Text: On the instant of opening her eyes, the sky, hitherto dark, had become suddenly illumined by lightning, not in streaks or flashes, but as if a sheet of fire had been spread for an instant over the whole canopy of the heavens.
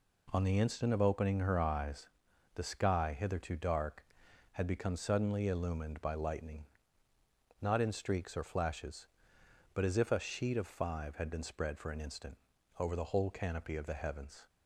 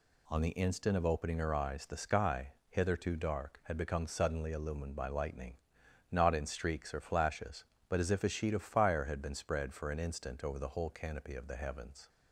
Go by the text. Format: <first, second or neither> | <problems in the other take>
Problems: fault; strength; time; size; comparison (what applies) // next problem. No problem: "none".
second | says "five" for "fire"; at 10.6 s // pauses between "instant" and "over"; at 12.3 s; 0.42 s long